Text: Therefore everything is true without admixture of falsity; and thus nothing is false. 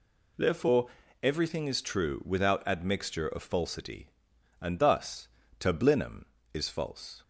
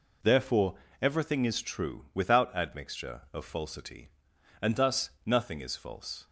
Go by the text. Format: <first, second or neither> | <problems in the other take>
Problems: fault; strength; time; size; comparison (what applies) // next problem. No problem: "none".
second | pauses between "Therefore" and "everything"; slight; at 0.8 s; 0.36 s long; slight in the second // says "tablinum" for "nothing"; at 5.5 s